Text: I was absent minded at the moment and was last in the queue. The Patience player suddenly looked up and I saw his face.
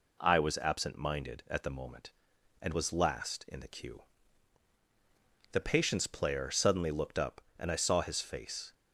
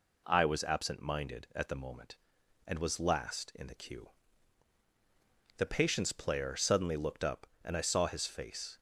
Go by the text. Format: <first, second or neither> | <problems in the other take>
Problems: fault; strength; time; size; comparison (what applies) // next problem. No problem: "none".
neither | none